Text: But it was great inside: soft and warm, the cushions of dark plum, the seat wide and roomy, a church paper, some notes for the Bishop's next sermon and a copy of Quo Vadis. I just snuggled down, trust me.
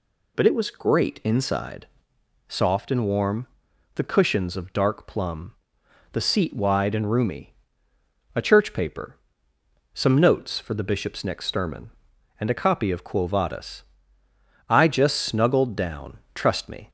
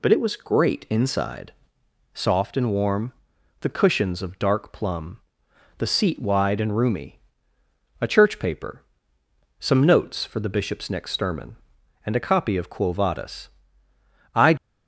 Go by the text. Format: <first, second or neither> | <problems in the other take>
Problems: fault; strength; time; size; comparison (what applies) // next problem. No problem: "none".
first | stops before "just snuggled down trust me"; at 14.5 s